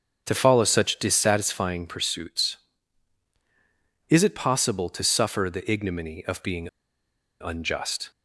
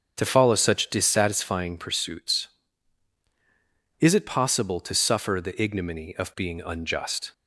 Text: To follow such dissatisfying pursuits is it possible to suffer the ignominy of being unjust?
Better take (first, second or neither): second